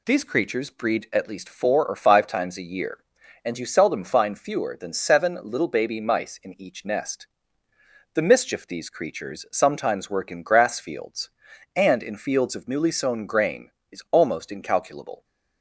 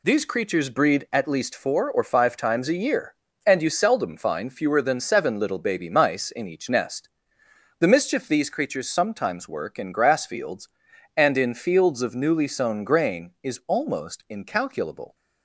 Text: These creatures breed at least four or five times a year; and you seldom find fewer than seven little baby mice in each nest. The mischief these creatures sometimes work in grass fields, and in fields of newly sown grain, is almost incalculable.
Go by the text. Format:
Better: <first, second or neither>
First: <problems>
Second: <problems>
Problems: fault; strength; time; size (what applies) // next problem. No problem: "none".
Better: neither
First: none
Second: none